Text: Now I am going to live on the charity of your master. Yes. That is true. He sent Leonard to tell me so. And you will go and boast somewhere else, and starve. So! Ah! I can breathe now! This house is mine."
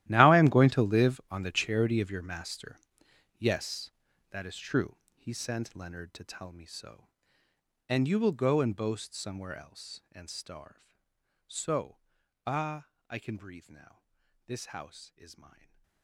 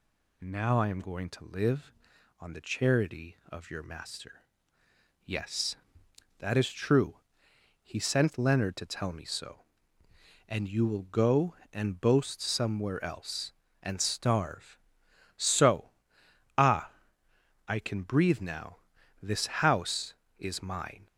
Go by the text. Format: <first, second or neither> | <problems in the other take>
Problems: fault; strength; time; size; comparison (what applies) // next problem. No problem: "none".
second | gets quieter; strong; throughout; 19 dB // stays silent after the last word; slight; from 15.4 s on; 0.6 s long